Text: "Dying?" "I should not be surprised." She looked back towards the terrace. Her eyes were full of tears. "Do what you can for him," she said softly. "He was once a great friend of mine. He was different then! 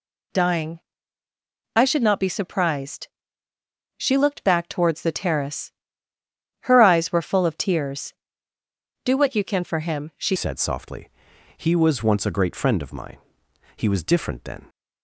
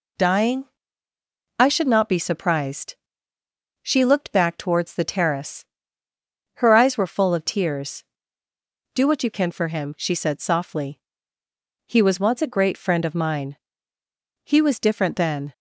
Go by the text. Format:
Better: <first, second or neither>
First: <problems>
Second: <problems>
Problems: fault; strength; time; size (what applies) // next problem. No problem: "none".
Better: second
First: changes voice at "said"; from 10.3 s on; 4.3 s long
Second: none